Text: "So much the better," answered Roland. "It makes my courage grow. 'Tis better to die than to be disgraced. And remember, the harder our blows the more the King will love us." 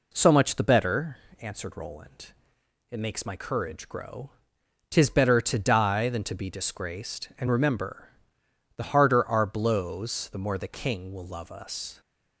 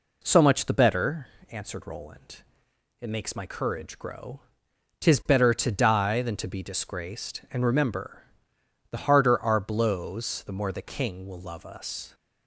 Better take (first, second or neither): neither